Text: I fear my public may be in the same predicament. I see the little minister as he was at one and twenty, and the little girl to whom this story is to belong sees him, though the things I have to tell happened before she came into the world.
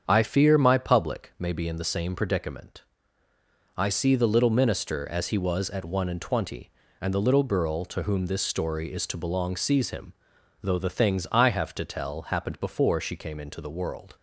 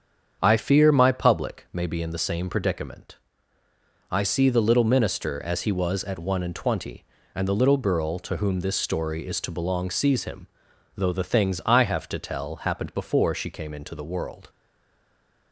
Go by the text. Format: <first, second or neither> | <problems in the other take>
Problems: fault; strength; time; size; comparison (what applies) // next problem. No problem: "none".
first | starts louder than the rest; strong; until 1.4 s; 7.5 dB; strong in the first // stays silent after the last word; from 14.4 s on; 1.1 s long